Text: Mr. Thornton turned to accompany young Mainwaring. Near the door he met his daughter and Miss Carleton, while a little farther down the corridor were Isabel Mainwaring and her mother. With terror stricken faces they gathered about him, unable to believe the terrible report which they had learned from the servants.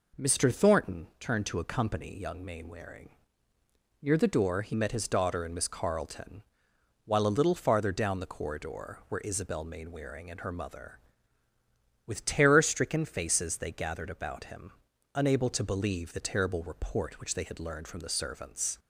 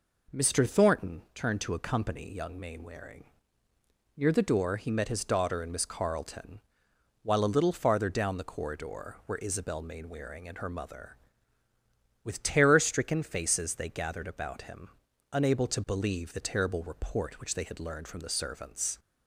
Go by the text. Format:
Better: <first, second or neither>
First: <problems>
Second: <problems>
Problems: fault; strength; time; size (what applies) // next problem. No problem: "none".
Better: neither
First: none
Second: none